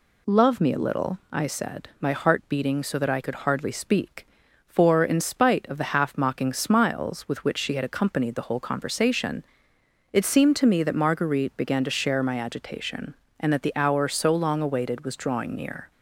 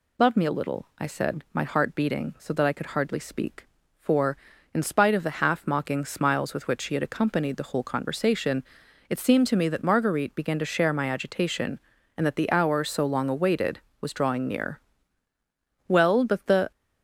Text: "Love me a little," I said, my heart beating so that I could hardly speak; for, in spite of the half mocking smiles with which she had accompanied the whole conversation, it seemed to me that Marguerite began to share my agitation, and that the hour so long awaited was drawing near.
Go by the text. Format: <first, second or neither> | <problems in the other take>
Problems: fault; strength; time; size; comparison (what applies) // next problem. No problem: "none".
first | goes on to say "Well but the"; noticeable; from 15.8 s on; 0.82 s long